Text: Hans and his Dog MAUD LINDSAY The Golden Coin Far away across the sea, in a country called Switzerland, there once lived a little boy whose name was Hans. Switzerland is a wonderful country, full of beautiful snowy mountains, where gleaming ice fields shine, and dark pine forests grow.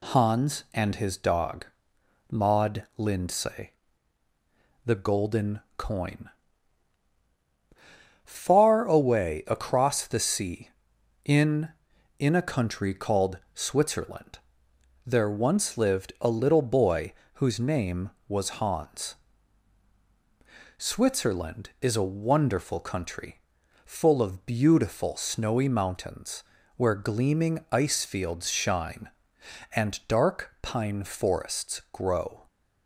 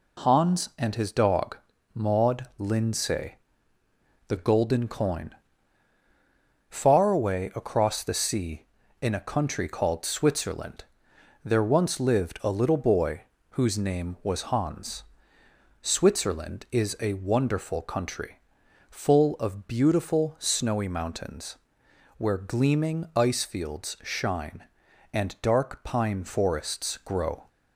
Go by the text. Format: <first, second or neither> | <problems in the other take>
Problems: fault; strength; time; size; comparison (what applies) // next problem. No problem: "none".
second | pauses between "Dog" and "MAUD"; noticeable; at 1.6 s; 0.64 s long; slight in the second // pauses between "LINDSAY" and "The"; at 3.7 s; 1.1 s long; noticeable in the second // pauses between "Golden" and "Coin"; slight; at 5.6 s; 0.16 s long // pauses between "Coin" and "Far"; strong; at 6.2 s; 1.9 s long; strong in the second // says "in" twice; at 12.1 s // pauses between "called" and "Switzerland"; slight; at 13.3 s; 0.16 s long // pauses between "boy" and "whose"; slight; at 17.1 s; 0.22 s long; slight in the second